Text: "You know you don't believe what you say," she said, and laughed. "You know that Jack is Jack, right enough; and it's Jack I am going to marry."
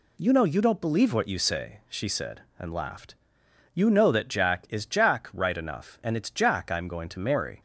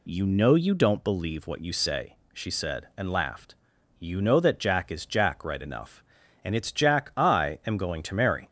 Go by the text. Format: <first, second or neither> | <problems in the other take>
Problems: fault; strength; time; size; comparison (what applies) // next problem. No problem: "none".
neither | none